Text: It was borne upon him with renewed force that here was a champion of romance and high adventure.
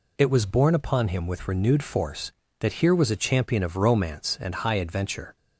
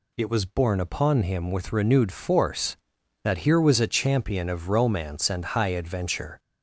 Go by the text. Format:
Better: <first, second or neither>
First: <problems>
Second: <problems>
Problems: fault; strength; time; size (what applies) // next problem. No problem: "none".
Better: first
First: none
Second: gets louder; slight; throughout; 2 dB